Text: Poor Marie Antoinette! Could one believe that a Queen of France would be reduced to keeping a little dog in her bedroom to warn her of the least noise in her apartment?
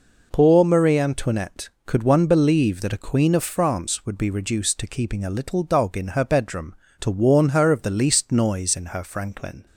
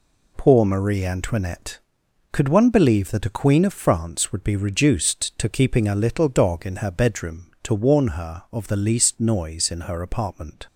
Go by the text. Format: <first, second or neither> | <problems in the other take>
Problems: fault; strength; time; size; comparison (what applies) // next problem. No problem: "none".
second | says "franklin" for "apartment"; at 9.0 s